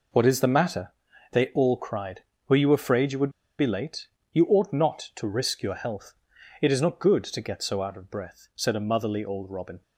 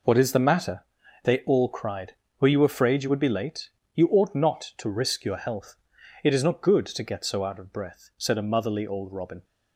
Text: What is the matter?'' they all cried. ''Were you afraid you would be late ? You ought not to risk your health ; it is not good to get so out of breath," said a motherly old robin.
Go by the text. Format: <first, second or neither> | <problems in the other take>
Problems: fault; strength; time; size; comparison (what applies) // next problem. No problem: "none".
second | pauses between "would" and "be"; slight; at 3.3 s; 0.28 s long